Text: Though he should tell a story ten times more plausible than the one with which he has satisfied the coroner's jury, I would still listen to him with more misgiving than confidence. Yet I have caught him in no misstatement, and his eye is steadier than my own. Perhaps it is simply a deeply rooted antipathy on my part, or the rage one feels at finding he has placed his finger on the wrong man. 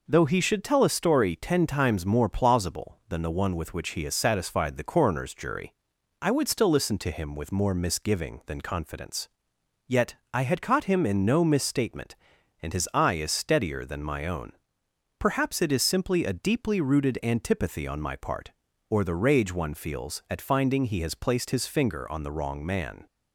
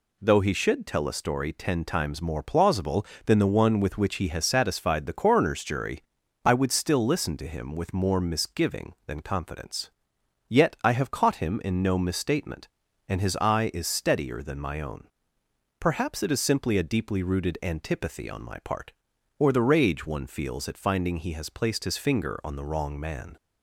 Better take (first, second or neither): second